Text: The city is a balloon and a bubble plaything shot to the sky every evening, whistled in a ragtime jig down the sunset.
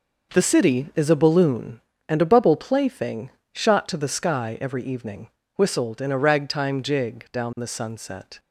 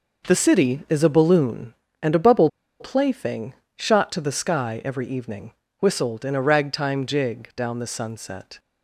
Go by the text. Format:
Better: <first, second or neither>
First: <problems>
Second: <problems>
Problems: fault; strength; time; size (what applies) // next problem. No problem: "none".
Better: first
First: pauses between "plaything" and "shot"; slight; at 3.3 s; 0.24 s long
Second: pauses between "bubble" and "plaything"; slight; at 2.4 s; 0.31 s long // pauses between "plaything" and "shot"; slight; at 3.5 s; 0.24 s long